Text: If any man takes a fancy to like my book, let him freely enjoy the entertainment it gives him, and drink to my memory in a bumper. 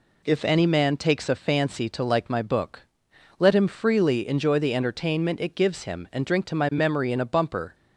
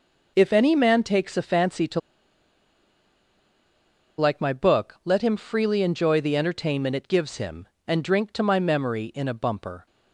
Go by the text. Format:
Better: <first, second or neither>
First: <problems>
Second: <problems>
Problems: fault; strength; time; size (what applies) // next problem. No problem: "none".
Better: first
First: none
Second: pauses between "to" and "like"; strong; at 1.9 s; 2.1 s long